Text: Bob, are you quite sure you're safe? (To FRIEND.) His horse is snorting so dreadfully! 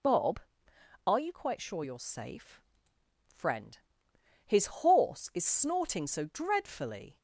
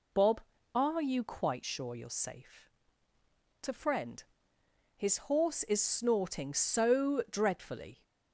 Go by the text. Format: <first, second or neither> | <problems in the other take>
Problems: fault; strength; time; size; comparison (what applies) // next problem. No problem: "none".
second | skips "To"; at 2.9 s